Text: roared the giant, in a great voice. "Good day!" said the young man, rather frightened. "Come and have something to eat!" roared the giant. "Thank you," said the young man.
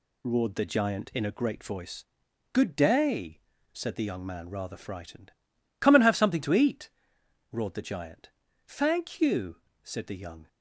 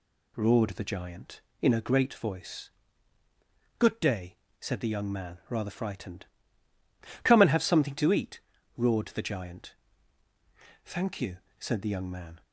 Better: second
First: stops before "man"; at 10.4 s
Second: none

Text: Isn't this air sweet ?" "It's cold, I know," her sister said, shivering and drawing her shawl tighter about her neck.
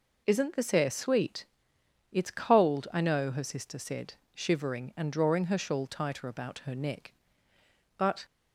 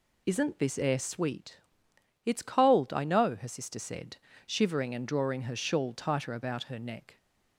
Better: second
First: goes on to say "But"; slight; from 7.9 s on; 0.26 s long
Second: none

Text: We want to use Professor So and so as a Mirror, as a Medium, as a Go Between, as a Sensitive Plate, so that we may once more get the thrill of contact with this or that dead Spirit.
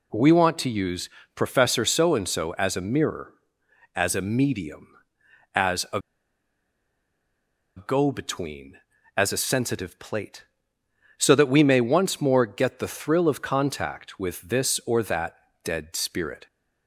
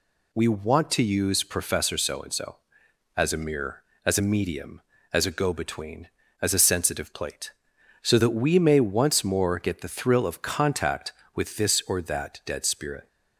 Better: second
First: pauses between "use" and "Professor"; slight; at 1.0 s; 0.26 s long // pauses between "a" and "Go"; strong; at 6.0 s; 1.7 s long // pauses between "that" and "dead"; slight; at 15.3 s; 0.26 s long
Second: none

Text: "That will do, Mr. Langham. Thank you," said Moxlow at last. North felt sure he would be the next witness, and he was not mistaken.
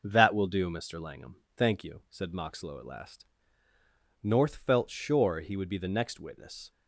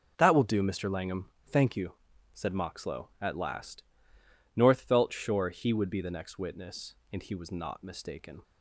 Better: second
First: stops before "and he was not mistaken"; at 6.7 s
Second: none

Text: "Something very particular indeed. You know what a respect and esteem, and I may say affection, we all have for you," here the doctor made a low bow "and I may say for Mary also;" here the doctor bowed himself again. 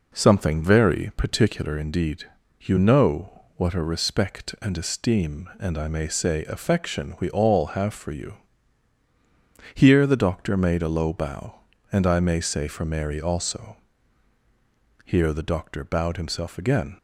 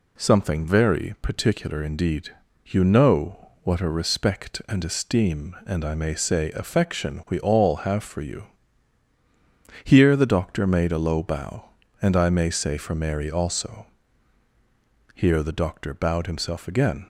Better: second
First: starts louder than the rest; noticeable; until 1.9 s; 4.5 dB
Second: none

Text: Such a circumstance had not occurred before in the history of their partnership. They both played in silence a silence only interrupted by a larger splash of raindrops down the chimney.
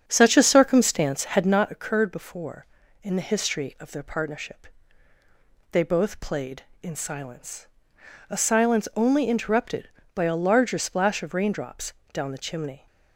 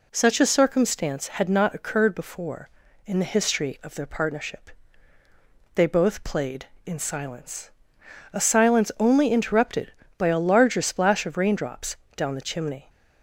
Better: second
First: starts louder than the rest; strong; until 1.7 s; 7.5 dB // pauses between "silence" and "a"; noticeable; at 7.6 s; 0.62 s long // pauses between "raindrops" and "down"; slight; at 11.9 s; 0.18 s long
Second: pauses between "silence" and "a"; noticeable; at 7.6 s; 0.62 s long // pauses between "raindrops" and "down"; slight; at 11.9 s; 0.18 s long

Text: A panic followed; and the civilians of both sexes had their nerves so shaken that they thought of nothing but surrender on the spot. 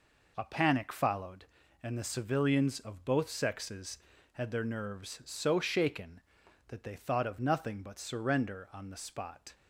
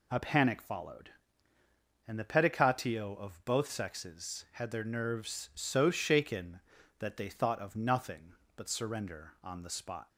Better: first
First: none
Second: says "pedicatio" for "civilians"; at 2.2 s

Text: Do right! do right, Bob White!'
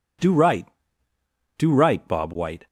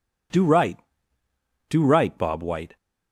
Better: neither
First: none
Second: none

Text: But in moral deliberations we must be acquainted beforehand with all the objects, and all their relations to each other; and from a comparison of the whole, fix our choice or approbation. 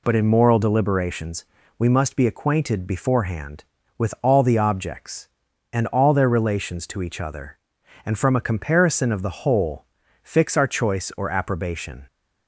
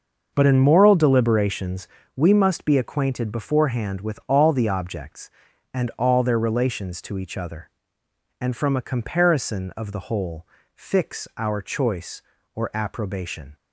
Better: first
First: pauses between "deliberations" and "we"; slight; at 1.4 s; 0.30 s long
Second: starts louder than the rest; noticeable; until 2.0 s; 6 dB // pauses between "deliberations" and "we"; slight; at 1.8 s; 0.30 s long

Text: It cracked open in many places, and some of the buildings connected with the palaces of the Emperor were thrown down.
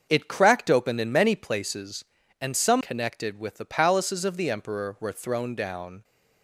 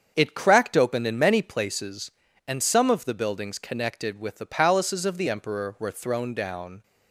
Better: second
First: starts louder than the rest; until 1.1 s; 6.5 dB // skips "of the buildings"; at 2.8 s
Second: starts louder than the rest; strong; until 1.1 s; 7 dB

